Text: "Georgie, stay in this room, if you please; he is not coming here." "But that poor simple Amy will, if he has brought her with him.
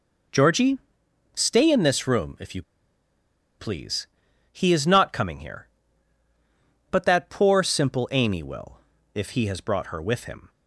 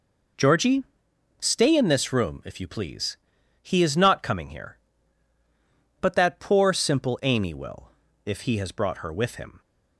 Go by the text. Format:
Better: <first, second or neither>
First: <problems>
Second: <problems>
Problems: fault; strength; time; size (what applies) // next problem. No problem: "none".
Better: second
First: pauses between "you" and "please"; noticeable; at 2.6 s; 0.96 s long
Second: none